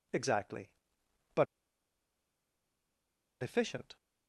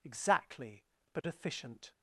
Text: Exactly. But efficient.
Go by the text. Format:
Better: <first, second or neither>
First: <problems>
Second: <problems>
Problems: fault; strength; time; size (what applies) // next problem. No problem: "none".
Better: second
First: pauses between "But" and "efficient"; strong; at 1.4 s; 1.9 s long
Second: none